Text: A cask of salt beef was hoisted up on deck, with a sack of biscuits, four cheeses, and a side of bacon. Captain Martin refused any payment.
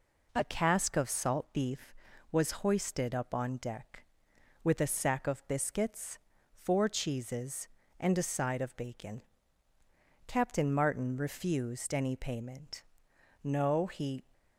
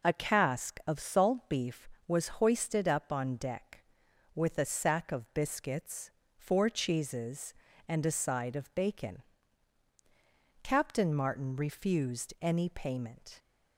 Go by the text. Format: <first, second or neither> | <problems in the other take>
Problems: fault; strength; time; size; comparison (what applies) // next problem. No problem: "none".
second | goes on to say "No he"; noticeable; from 13.4 s on; 0.80 s long